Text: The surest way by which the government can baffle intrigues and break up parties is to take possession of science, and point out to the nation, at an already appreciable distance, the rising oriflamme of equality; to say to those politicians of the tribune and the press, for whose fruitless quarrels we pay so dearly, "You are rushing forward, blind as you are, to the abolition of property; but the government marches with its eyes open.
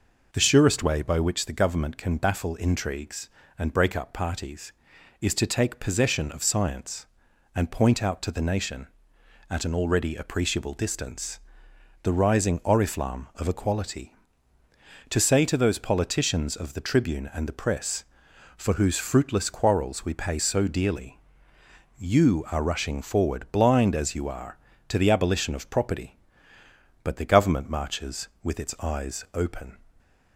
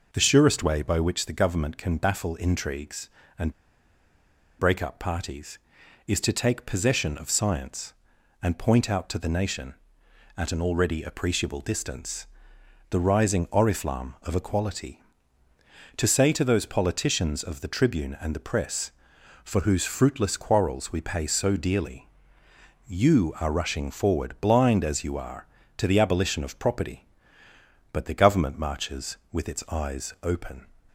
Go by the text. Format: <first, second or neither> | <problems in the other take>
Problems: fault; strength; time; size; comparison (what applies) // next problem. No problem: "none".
first | pauses between "and" and "break"; at 3.5 s; 1.0 s long